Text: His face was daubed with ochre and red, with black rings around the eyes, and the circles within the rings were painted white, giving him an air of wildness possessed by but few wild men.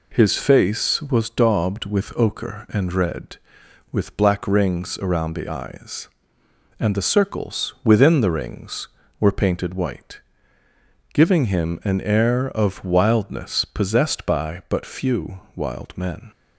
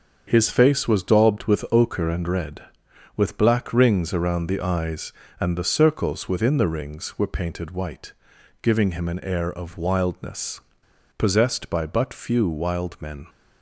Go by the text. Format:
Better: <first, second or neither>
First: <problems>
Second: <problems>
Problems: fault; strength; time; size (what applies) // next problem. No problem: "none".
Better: first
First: none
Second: starts louder than the rest; strong; until 1.2 s; 7 dB // pauses between "wildness" and "possessed"; noticeable; at 10.6 s; 0.57 s long